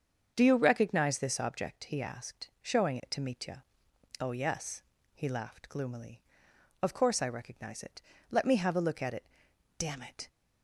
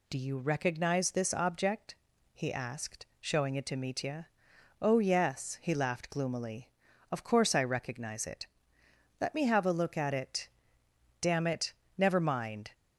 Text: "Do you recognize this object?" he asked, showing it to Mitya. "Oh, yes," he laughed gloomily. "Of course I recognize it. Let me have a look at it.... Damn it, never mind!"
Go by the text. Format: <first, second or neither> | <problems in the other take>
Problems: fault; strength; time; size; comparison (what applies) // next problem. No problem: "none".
second | starts louder than the rest; until 1.3 s; 7 dB // stops before "never mind"; at 10.2 s